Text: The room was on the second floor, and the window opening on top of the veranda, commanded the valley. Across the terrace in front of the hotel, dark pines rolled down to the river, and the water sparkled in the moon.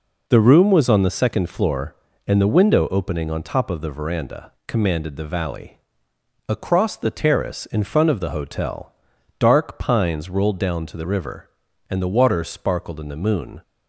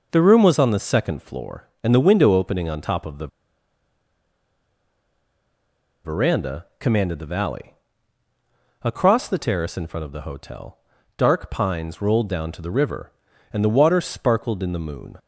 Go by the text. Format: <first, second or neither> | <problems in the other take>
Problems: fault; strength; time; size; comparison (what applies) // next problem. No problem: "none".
first | pauses between "the" and "veranda"; strong; at 3.2 s; 2.7 s long